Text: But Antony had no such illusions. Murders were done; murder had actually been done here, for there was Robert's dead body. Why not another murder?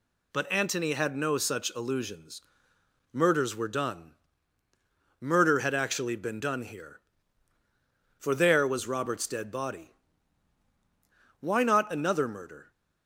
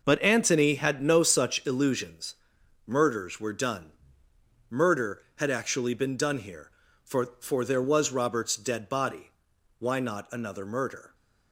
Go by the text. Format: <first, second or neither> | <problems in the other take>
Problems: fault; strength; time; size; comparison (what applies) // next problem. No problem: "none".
first | says "for" twice; at 7.3 s